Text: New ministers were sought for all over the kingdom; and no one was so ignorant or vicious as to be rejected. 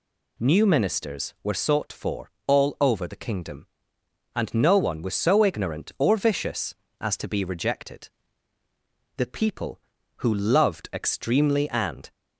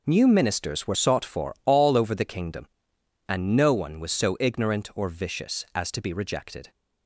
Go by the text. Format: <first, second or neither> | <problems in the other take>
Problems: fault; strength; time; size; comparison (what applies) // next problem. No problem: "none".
second | pauses between "for" and "all"; slight; at 2.2 s; 0.16 s long // goes on to say "The people who loved extremely and"; strong; from 9.1 s on; 2.9 s long